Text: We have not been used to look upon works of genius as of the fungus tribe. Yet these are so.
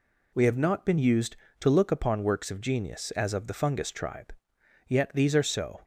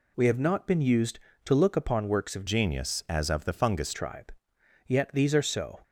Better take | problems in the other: first | changes voice from "genius" to "fungus"; from 2.4 to 3.9 s; 1.5 s long

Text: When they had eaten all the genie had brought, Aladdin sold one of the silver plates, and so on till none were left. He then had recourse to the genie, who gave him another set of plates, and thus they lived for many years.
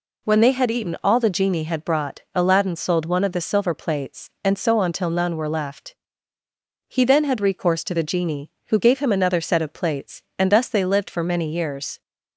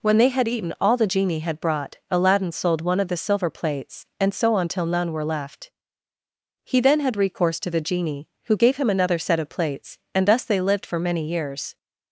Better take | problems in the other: neither | none

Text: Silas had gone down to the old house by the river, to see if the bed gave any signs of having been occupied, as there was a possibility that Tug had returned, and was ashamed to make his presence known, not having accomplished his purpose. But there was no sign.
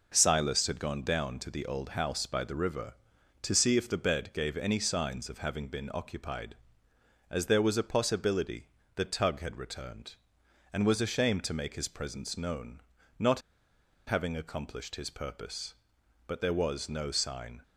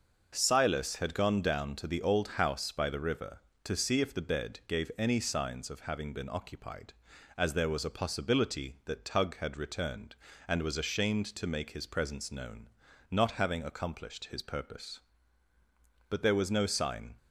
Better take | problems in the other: second | pauses between "not" and "having"; noticeable; at 13.4 s; 0.66 s long

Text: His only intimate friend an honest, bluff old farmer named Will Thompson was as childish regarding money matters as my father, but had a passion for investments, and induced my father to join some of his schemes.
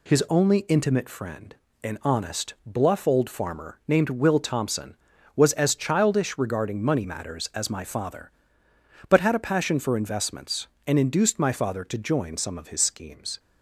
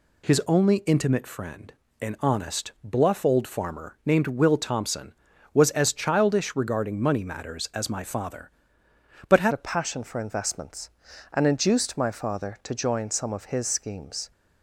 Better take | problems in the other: first | pauses between "friend" and "an"; slight; at 1.7 s; 0.26 s long; slight in the first // changes voice at "a"; from 9.5 s on; 4.8 s long

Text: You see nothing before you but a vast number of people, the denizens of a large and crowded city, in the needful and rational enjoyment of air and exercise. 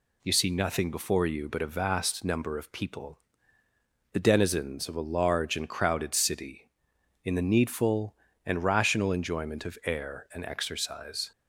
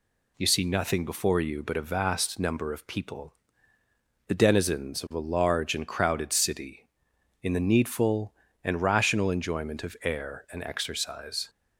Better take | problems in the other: neither | none

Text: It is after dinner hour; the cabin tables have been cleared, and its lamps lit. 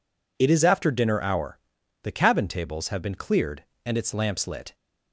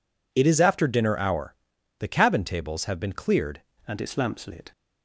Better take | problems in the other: first | changes voice at "and"; from 3.8 s on; 0.9 s long

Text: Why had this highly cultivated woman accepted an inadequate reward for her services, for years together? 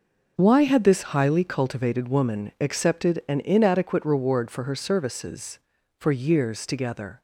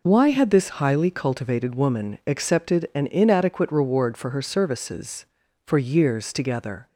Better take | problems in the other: second | gets quieter; strong; throughout; 9.5 dB

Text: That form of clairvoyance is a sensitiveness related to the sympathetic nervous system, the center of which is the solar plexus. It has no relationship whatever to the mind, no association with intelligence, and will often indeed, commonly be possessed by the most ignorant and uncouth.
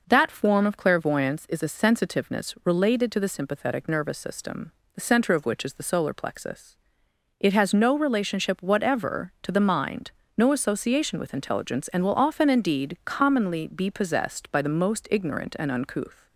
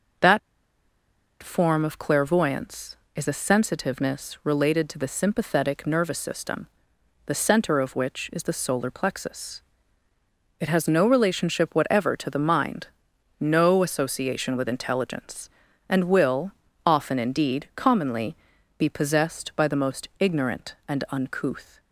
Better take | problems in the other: first | pauses between "That" and "form"; at 0.3 s; 1.0 s long // pauses between "will" and "often"; slight; at 16.5 s; 0.34 s long // pauses between "commonly" and "be"; at 18.3 s; 0.44 s long

